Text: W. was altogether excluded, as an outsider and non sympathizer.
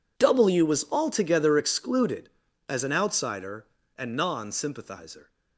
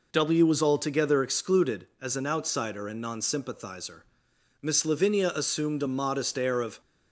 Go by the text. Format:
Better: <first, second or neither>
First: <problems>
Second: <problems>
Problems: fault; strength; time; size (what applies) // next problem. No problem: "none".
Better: first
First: none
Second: goes on to say "Miss Lavinia assumed a modest air of"; strong; from 4.5 s on; 2.2 s long